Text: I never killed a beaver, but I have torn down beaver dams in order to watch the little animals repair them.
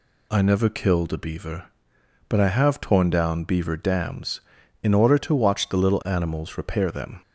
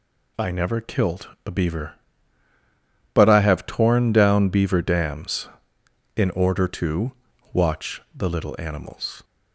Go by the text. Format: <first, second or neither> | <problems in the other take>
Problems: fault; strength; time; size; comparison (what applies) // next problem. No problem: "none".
first | pauses between "killed" and "a"; slight; at 1.2 s; 0.18 s long // pauses between "to" and "watch"; at 7.1 s; 0.42 s long // pauses between "watch" and "the"; slight; at 7.9 s; 0.16 s long // stops before "repair them"; at 9.2 s